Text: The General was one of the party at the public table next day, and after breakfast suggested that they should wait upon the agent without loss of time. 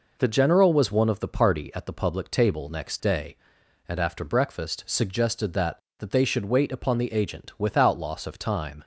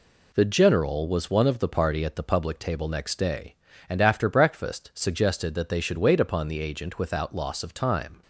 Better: second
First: says "that" twice; at 5.9 s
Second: none

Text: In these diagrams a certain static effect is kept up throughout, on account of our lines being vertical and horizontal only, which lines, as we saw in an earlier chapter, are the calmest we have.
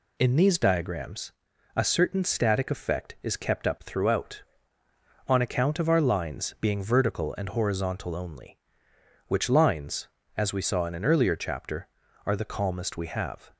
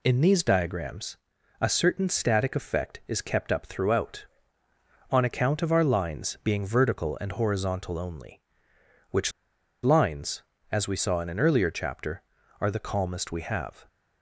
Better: first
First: pauses between "diagrams" and "a"; at 1.3 s; 0.44 s long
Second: pauses between "diagrams" and "a"; at 1.1 s; 0.44 s long // pauses between "which" and "lines"; noticeable; at 9.3 s; 0.52 s long

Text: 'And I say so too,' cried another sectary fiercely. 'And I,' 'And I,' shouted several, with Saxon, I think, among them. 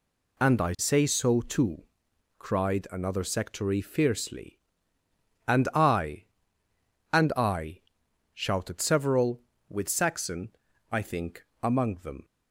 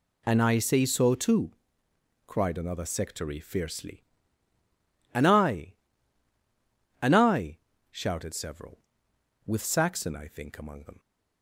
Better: neither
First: none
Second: none

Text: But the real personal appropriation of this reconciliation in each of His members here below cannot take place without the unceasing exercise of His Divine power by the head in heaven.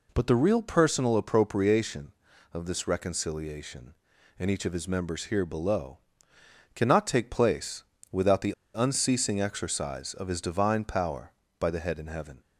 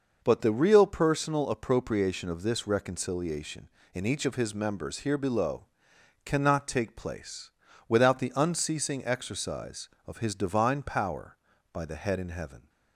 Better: second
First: pauses between "below" and "cannot"; noticeable; at 5.9 s; 0.76 s long // pauses between "place" and "without"; slight; at 7.8 s; 0.28 s long // pauses between "the" and "unceasing"; slight; at 8.5 s; 0.22 s long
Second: pauses between "below" and "cannot"; noticeable; at 5.6 s; 0.60 s long // pauses between "place" and "without"; at 7.4 s; 0.38 s long

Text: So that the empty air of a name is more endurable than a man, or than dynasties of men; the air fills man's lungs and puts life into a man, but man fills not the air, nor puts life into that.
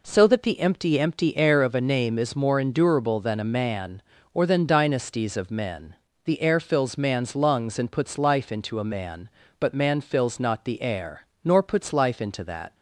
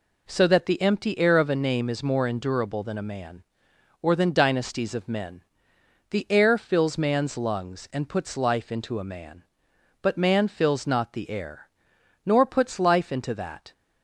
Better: second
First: says "empty" twice; at 1.0 s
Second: none

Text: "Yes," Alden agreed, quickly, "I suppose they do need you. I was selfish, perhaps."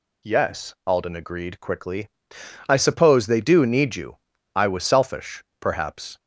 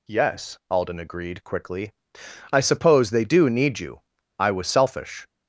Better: first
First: none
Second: stops before "perhaps"; at 5.2 s

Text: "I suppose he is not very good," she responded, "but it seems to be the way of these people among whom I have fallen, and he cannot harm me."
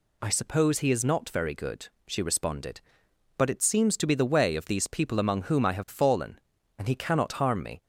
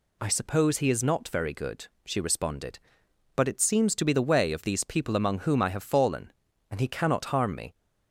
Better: neither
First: none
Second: none

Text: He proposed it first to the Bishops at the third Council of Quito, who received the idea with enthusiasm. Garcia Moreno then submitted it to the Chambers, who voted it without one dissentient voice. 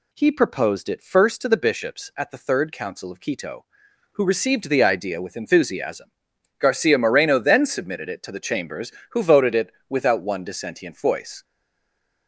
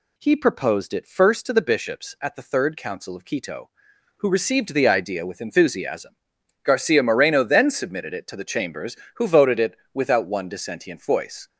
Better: second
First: pauses between "it" and "without"; slight; at 9.7 s; 0.18 s long // stays silent after the last word; slight; from 11.4 s on; 0.8 s long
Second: pauses between "it" and "without"; slight; at 9.7 s; 0.18 s long

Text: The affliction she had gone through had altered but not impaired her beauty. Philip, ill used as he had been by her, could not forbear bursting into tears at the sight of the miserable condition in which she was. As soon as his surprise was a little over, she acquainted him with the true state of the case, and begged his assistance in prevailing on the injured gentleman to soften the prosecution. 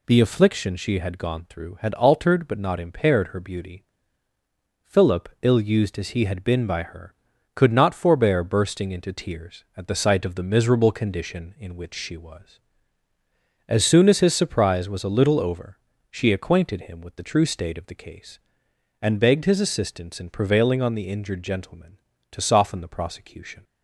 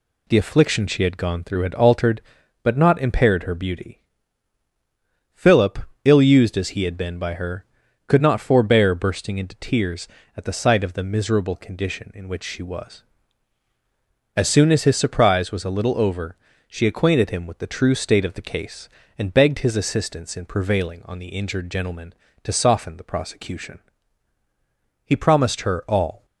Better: first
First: none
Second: goes on to say "He promised her all"; noticeable; from 25.0 s on; 1.2 s long

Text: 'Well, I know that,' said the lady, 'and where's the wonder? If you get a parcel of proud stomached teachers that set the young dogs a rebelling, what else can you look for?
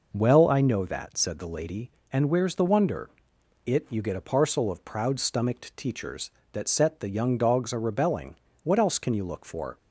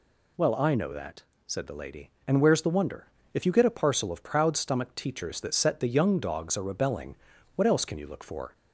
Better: second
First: says "It" for "If"; at 3.6 s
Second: none

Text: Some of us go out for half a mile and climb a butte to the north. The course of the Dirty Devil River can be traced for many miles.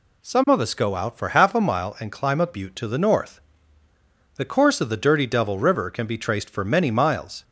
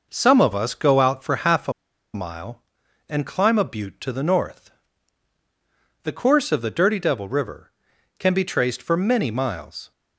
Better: first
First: none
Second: pauses between "a" and "mile"; at 1.7 s; 0.42 s long

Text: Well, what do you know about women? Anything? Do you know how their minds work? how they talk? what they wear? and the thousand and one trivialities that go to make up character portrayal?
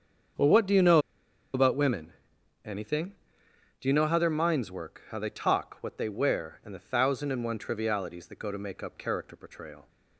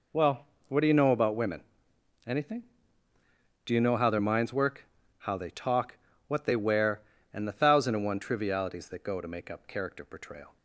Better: second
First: starts louder than the rest; strong; until 1.9 s; 7.5 dB // pauses between "know" and "about"; noticeable; at 0.9 s; 0.55 s long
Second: none

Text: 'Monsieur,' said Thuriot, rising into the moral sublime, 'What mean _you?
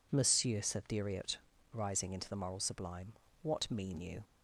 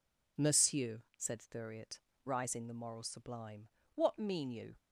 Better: first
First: none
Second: skips "into"; at 2.6 s

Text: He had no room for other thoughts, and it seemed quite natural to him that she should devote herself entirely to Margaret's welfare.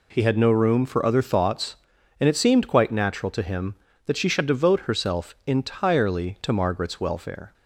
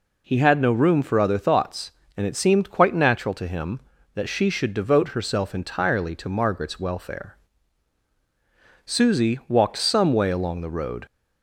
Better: first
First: none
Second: goes on to say "Susie walked some way along the road"; strong; from 8.8 s on; 2.2 s long

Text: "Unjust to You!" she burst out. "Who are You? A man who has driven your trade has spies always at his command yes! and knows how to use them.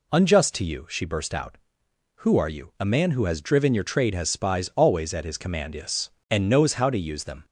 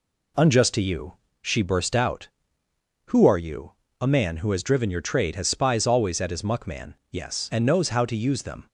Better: first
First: none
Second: says "muckman" for "command"; at 6.4 s

